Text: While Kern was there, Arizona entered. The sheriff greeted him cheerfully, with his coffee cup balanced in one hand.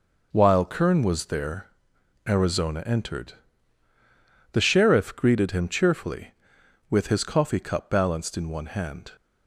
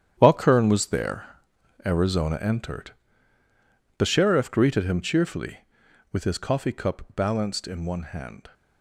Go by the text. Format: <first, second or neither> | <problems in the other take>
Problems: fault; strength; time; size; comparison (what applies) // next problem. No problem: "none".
first | gets quieter; strong; throughout; 11.5 dB